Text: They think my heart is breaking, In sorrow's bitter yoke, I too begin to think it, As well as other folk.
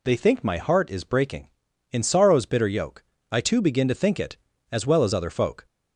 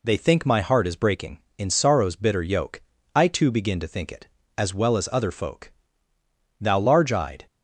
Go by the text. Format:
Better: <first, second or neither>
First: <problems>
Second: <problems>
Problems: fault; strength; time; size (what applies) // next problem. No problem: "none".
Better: first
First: none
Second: goes on to say "Thou large eyed"; noticeable; from 6.5 s on; 0.86 s long